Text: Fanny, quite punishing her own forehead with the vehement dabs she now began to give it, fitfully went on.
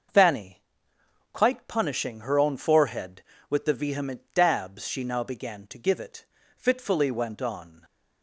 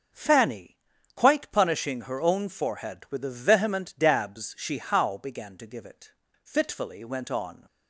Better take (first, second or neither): first